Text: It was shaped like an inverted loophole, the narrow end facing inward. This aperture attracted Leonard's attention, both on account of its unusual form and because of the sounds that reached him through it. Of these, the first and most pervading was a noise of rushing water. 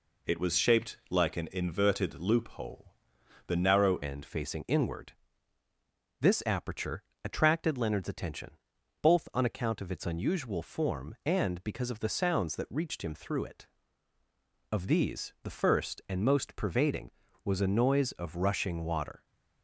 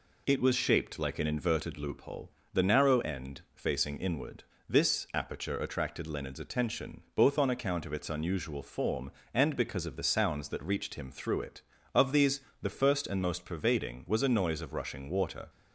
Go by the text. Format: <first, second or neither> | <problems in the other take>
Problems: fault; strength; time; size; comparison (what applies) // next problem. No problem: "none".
second | changes voice at "end"; from 4.0 s on; 15.2 s long // pauses between "aperture" and "attracted"; slight; at 7.0 s; 0.20 s long